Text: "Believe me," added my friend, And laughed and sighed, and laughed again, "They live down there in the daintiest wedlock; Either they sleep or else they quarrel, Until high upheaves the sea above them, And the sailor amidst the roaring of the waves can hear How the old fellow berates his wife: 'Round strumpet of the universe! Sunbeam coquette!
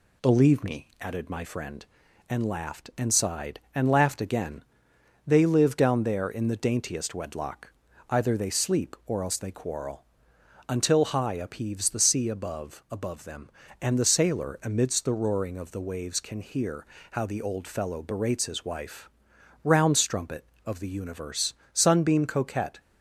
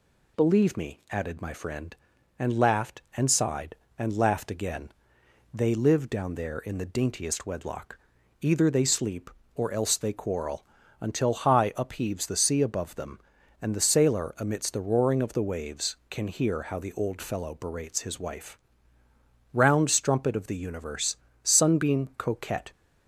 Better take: second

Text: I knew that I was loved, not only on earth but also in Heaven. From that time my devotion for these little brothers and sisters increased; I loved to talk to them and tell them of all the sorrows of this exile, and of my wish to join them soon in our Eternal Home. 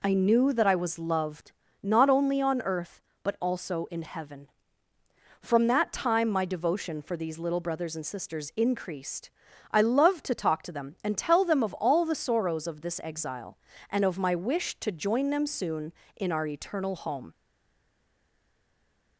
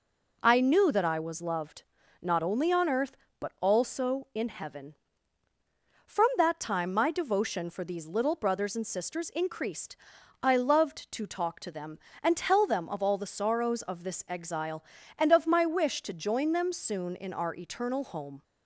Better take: second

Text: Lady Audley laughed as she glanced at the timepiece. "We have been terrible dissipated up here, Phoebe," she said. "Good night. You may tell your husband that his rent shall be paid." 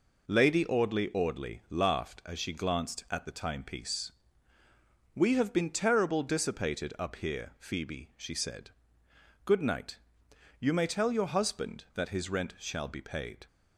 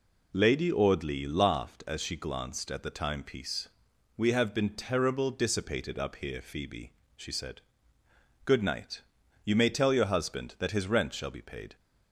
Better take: second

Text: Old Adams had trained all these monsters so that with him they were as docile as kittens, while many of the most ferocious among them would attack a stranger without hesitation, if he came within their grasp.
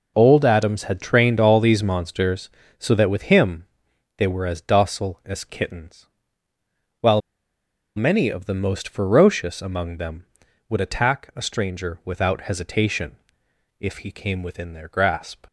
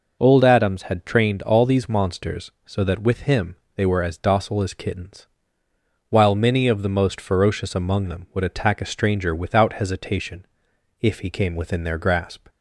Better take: second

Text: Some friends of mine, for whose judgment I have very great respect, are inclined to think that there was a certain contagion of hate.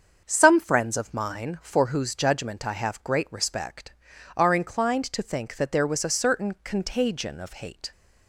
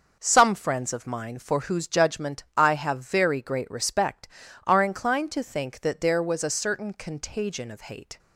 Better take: second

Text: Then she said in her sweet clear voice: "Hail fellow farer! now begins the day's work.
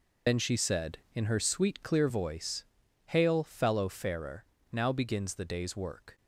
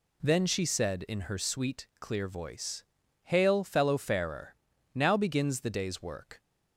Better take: second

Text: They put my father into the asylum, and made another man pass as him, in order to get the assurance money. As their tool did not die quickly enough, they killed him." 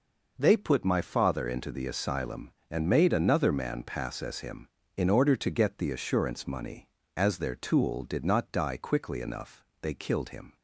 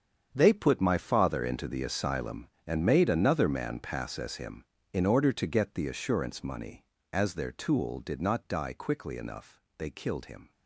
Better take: first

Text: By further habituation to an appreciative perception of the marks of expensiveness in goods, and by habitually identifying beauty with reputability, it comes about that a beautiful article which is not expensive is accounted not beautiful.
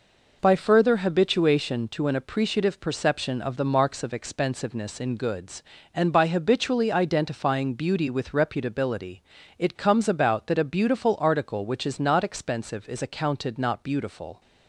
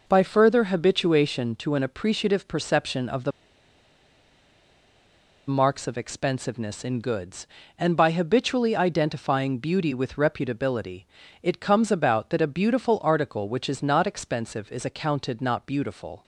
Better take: first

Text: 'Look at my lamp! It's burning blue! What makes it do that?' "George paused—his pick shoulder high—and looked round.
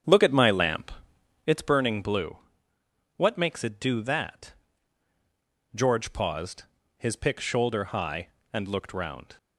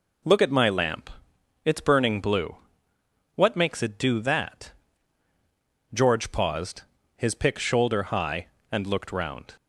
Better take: second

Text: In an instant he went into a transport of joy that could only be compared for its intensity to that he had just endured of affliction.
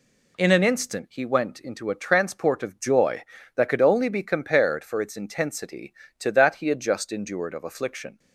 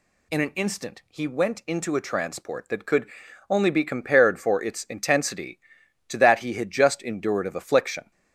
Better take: first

